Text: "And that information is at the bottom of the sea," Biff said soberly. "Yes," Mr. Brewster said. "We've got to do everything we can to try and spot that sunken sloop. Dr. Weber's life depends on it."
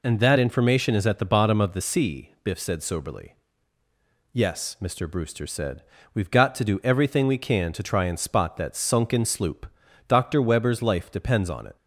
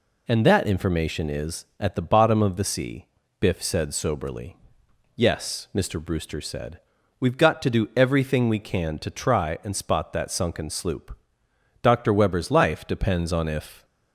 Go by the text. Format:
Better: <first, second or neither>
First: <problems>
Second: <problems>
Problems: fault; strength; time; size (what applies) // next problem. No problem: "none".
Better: first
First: none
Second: says "if" for "it"; at 13.4 s